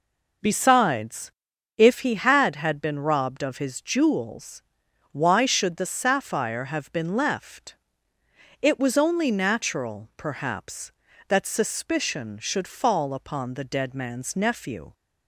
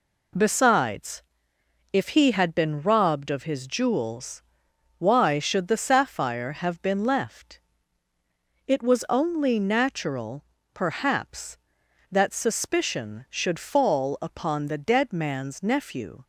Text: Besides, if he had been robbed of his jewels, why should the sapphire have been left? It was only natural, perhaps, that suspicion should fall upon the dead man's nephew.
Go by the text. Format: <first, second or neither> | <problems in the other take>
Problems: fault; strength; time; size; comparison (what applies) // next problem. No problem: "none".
second | says "had" twice; at 2.5 s